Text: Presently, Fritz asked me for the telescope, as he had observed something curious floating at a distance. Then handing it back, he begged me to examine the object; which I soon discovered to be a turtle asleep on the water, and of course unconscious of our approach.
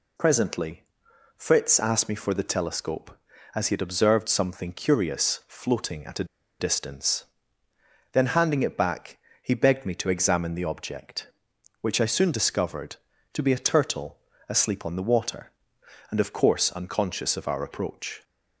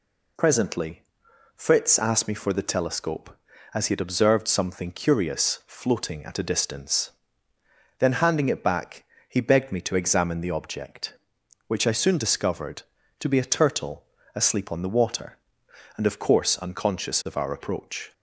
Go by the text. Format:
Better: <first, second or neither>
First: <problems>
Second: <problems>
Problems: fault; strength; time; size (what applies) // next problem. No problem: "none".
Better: second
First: pauses between "a" and "distance"; slight; at 6.2 s; 0.35 s long // pauses between "turtle" and "asleep"; slight; at 14.1 s; 0.32 s long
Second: pauses between "turtle" and "asleep"; slight; at 14.0 s; 0.32 s long